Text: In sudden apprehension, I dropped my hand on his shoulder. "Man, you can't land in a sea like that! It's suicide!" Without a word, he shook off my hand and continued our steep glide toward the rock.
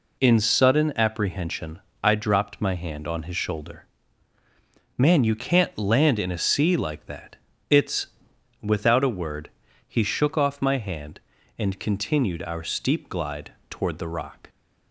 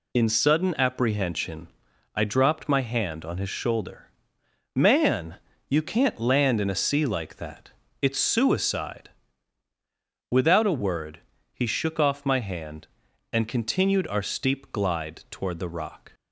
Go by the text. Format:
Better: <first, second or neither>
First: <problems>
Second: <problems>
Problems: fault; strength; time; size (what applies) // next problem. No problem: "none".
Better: second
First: skips "suicide"; at 8.3 s // pauses between "glide" and "toward"; slight; at 13.5 s; 0.16 s long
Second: none